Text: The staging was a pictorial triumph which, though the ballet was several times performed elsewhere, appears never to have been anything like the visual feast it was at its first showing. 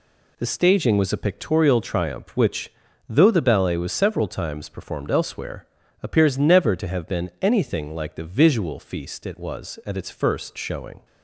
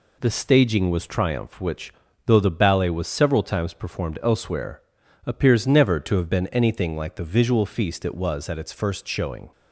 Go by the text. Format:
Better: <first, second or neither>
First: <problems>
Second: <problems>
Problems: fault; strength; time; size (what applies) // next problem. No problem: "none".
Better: first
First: none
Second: skips "a pictorial"; at 1.0 s